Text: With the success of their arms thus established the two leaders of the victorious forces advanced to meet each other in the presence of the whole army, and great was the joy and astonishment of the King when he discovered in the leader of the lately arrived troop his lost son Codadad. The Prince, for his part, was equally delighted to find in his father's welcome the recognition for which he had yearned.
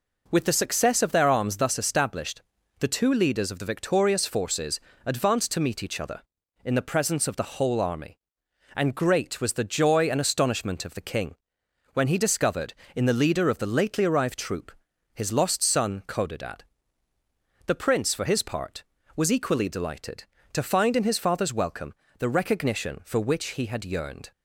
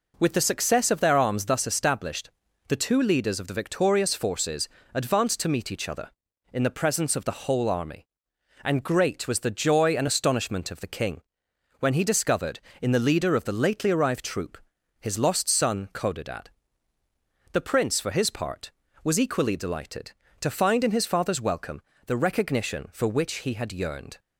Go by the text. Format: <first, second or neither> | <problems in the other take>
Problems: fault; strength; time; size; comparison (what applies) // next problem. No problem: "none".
neither | pauses between "established" and "the"; the same in both // pauses between "forces" and "advanced"; slight; the same in both // pauses between "King" and "when"; noticeable; the same in both // pauses between "troop" and "his"; the same in both // pauses between "welcome" and "the"; slight; the same in both